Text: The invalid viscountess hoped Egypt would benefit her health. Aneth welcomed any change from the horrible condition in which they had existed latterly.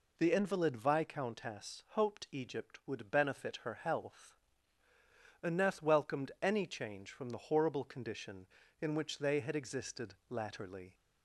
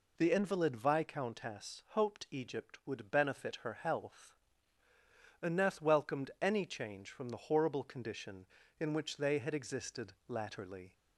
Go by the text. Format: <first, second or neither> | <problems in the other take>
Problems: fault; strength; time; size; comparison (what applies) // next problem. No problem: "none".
neither | pauses between "existed" and "latterly"; slight; the same in both